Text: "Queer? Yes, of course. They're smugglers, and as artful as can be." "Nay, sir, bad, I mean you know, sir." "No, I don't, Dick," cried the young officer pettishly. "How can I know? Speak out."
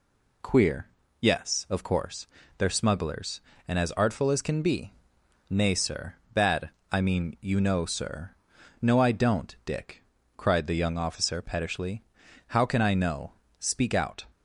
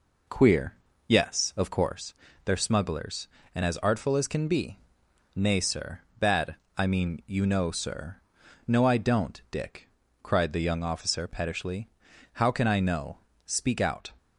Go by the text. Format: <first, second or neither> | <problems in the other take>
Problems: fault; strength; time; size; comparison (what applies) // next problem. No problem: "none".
first | starts louder than the rest; noticeable; until 2.0 s; 4 dB